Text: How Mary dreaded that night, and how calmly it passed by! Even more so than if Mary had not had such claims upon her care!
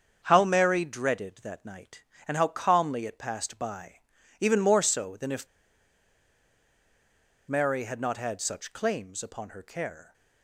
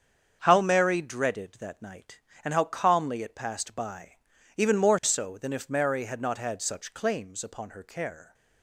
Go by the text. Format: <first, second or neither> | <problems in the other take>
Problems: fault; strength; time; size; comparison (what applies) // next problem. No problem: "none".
second | starts louder than the rest; strong; until 1.2 s; 7 dB; strong in the second // pauses between "if" and "Mary"; strong; at 5.4 s; 2.0 s long